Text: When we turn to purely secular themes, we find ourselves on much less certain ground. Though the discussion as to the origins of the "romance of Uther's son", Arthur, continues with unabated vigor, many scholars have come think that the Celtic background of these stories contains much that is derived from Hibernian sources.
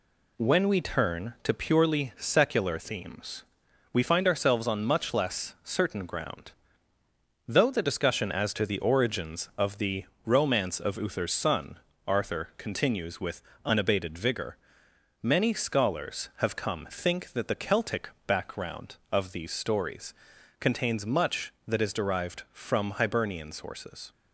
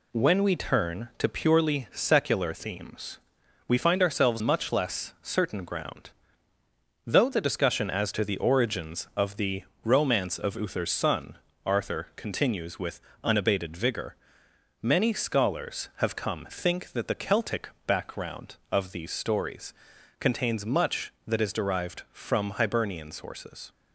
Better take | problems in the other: first | skips "on"; at 4.4 s // pauses between "the" and "romance"; slight; at 9.6 s; 0.22 s long; slight in the first // pauses between "with" and "unabated"; slight; at 13.0 s; 0.22 s long; slight in the first // pauses between "Celtic" and "background"; slight; at 17.6 s; 0.18 s long; slight in the first // pauses between "stories" and "contains"; noticeable; at 19.7 s; 0.46 s long; noticeable in the first

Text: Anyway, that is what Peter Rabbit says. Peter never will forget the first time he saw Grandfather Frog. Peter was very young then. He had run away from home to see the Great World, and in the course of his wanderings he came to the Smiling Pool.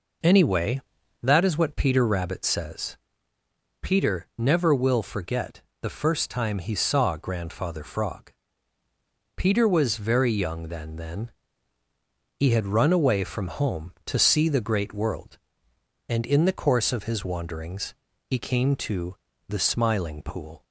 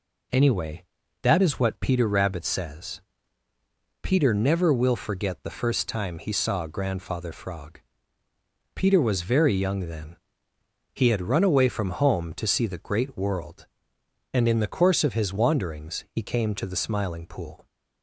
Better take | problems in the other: second | pauses between "forget" and "the"; slight; at 5.6 s; 0.20 s long // says "then" twice; at 10.9 s // pauses between "wanderings" and "he"; slight; at 17.9 s; 0.34 s long // pauses between "to" and "the"; slight; at 19.1 s; 0.34 s long

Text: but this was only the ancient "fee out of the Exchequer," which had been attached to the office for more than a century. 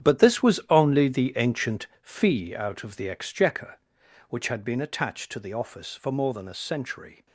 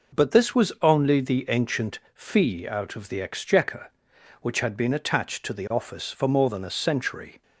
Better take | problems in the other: second | gets quieter; strong; throughout; 13.5 dB // pauses between "ancient" and "fee"; slight; at 1.8 s; 0.16 s long; slight in the second

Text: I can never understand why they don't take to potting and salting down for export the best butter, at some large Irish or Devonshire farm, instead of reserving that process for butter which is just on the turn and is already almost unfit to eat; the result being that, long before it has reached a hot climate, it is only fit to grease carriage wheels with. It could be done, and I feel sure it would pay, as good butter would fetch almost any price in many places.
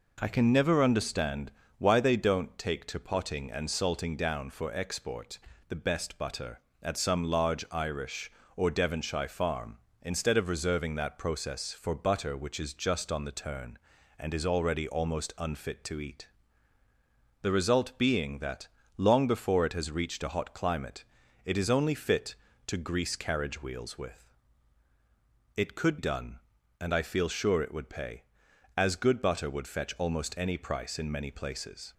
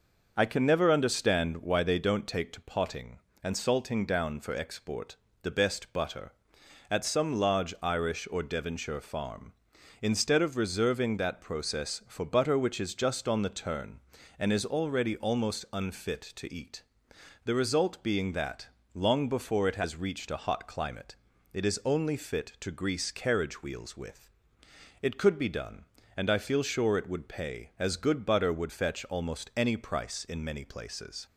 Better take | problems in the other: second | pauses between "understand" and "why"; slight; at 1.5 s; 0.26 s long // pauses between "export" and "the"; slight; at 5.3 s; 0.30 s long; slight in the second // skips "be"; at 25.9 s

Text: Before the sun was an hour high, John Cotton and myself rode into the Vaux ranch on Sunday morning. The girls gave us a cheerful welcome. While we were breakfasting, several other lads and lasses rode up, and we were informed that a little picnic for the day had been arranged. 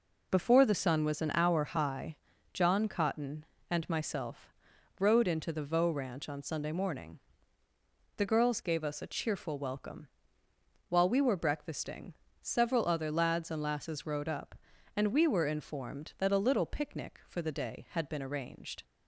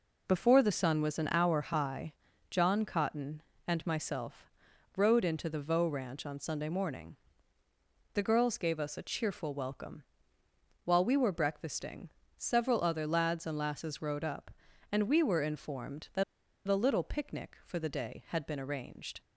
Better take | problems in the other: first | pauses between "myself" and "rode"; noticeable; at 4.5 s; 0.46 s long; noticeable in the first // pauses between "that" and "a"; at 16.2 s; 0.44 s long

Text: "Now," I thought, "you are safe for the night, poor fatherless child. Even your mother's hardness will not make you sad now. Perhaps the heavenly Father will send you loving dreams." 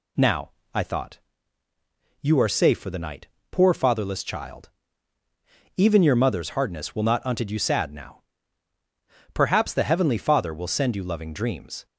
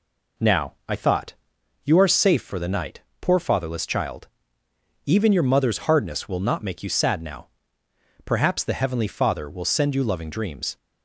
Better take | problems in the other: second | says "unted" for "make"; at 7.2 s

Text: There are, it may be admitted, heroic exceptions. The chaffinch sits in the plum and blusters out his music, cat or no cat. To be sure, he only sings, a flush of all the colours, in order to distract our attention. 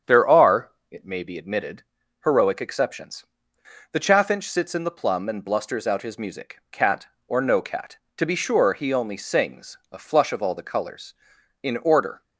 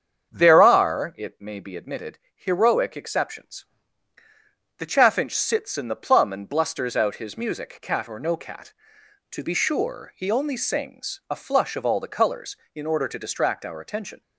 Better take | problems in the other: second | starts louder than the rest; strong; until 1.2 s; 8 dB; strong in the second // stops before "to distract our attention"; at 12.2 s

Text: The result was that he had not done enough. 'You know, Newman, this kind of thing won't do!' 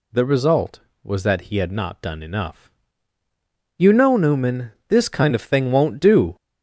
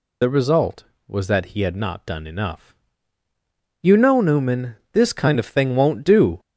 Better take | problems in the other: first | loses the start of "The"; at 0.2 s; 50 ms

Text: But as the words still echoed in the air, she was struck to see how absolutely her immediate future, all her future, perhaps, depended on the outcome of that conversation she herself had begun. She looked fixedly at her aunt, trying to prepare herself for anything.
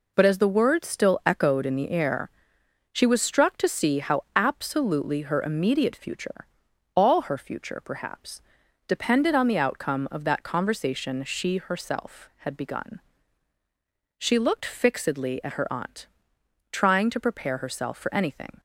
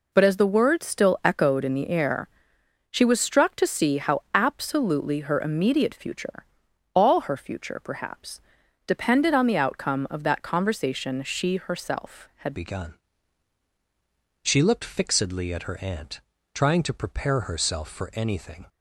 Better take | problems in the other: first | changes voice at "begun"; from 12.5 s on; 6.1 s long

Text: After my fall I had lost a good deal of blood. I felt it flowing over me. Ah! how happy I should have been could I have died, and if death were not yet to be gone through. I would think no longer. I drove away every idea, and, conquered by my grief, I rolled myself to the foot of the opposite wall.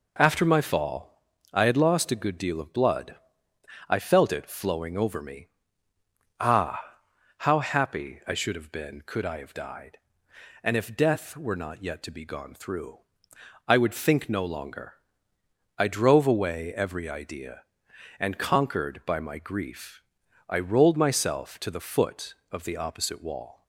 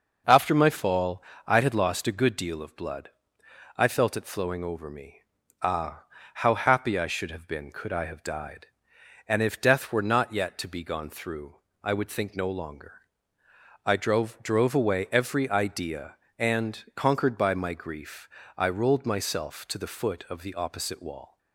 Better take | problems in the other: first | pauses between "fall" and "I"; slight; at 1.2 s; 0.24 s long; slight in the first // says "drove" twice; at 14.4 s

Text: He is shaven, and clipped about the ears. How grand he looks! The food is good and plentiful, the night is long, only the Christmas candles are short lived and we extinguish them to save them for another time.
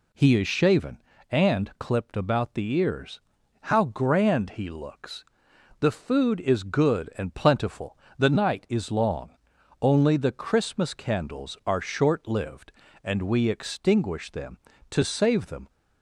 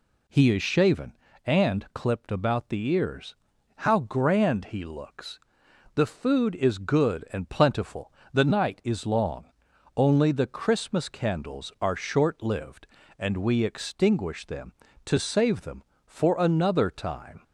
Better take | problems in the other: second | stops before "for another time"; at 15.6 s

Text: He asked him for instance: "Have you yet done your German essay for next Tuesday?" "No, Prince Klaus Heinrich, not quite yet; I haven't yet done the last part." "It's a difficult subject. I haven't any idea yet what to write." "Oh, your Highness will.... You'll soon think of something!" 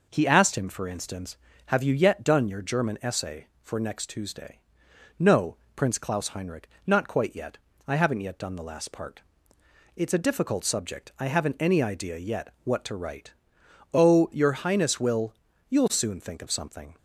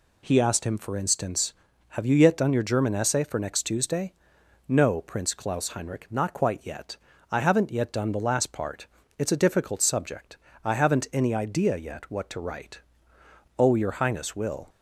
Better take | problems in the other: first | stops before "You'll soon think of something"; at 14.6 s

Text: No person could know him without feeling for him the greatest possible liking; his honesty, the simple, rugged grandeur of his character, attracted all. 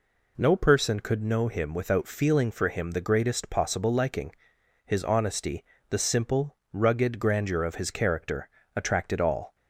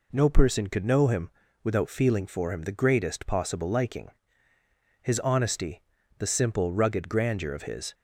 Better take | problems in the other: first | pauses between "him" and "without"; slight; at 1.2 s; 0.32 s long // stops before "character attracted all"; at 7.9 s

